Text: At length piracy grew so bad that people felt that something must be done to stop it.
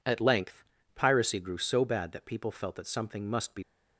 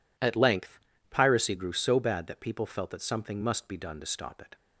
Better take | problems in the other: second | pauses between "length" and "piracy"; slight; at 0.6 s; 0.32 s long; slight in the second // stops before "done to stop it"; at 3.6 s

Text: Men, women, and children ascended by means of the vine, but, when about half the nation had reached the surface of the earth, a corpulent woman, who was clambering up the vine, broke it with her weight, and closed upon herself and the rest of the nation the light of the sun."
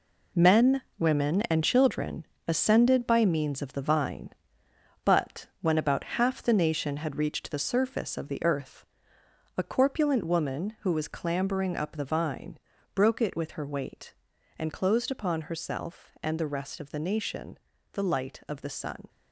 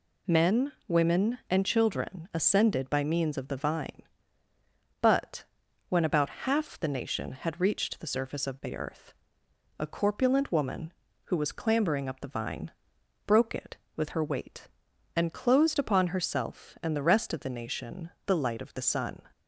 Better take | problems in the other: second | gets quieter; strong; throughout; 9.5 dB // pauses between "children" and "ascended"; slight; at 2.2 s; 0.22 s long // pauses between "nation" and "the"; slight; at 17.5 s; 0.34 s long; slight in the second

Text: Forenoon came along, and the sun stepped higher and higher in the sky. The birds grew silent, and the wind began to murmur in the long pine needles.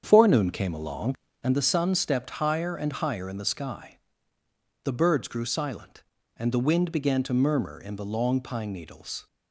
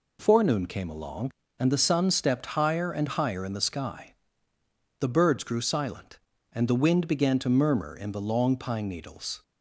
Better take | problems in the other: second | starts louder than the rest; strong; until 1.5 s; 7.5 dB

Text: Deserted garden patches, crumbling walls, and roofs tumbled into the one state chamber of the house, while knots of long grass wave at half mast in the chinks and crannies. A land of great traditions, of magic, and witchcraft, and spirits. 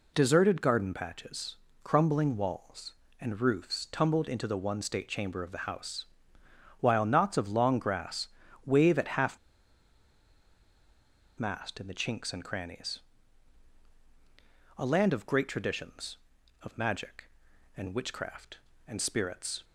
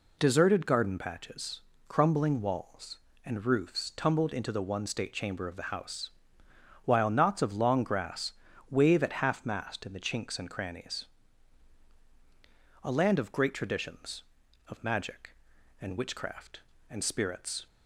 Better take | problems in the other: second | pauses between "grass" and "wave"; slight; at 8.2 s; 0.36 s long; slight in the second // pauses between "half" and "mast"; strong; at 9.3 s; 2.0 s long

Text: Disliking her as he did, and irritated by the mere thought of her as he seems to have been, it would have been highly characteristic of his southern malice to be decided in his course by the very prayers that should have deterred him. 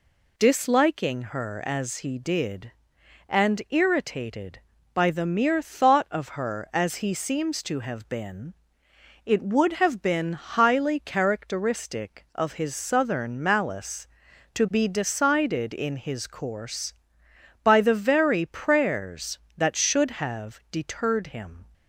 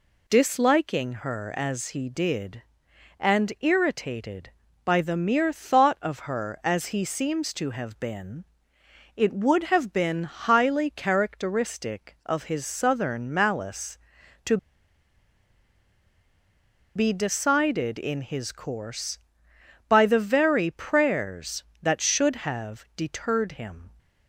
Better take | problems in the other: first | pauses between "to" and "be"; strong; at 14.5 s; 2.3 s long

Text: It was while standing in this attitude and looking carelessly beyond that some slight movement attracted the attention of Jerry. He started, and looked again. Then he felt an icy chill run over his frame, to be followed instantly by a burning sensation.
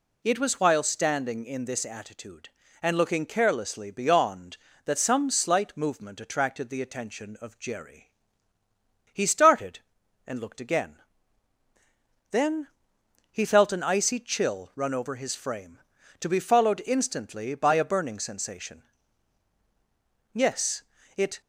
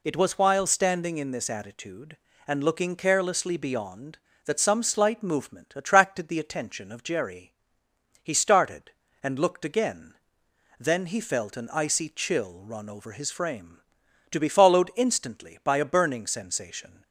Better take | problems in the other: second | pauses between "Then" and "he"; noticeable; at 12.6 s; 0.62 s long // goes on to say "Yes it"; noticeable; from 20.3 s on; 1.0 s long

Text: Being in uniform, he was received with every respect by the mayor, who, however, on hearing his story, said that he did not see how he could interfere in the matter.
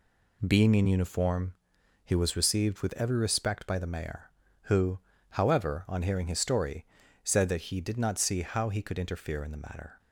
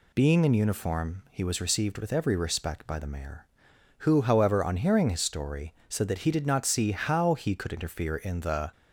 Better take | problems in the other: first | stops before "matter"; at 8.7 s

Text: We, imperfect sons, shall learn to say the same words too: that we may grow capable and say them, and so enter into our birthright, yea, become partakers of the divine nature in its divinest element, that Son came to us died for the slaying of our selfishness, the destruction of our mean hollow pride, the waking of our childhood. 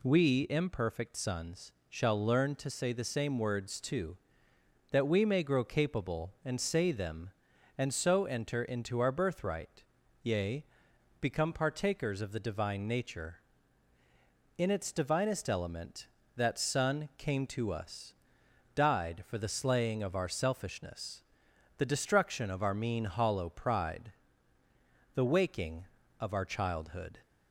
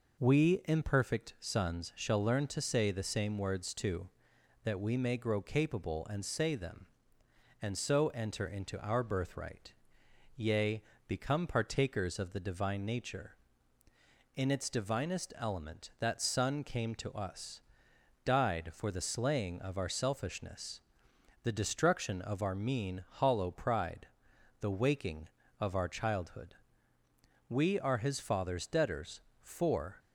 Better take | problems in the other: first | pauses between "us" and "died"; noticeable; at 17.6 s; 0.64 s long; noticeable in the first // goes on to say "We are his father's debtors for"; strong; from 27.4 s on; 2.5 s long

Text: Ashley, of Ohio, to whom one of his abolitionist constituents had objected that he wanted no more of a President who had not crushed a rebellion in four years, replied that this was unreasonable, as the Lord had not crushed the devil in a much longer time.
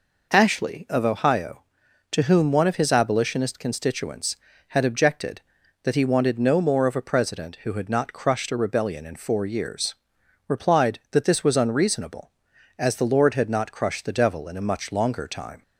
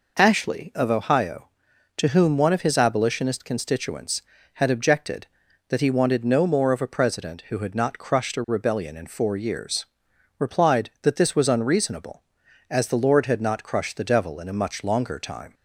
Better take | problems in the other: neither | none

